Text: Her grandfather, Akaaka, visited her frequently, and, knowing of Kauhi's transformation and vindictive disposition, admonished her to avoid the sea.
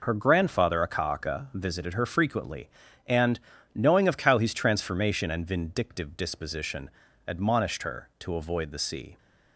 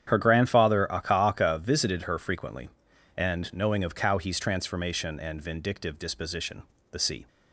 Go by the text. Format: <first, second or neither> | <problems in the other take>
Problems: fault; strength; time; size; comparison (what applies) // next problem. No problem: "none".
first | starts louder than the rest; strong; until 1.1 s; 9 dB // skips "admonished her to avoid"; at 6.7 s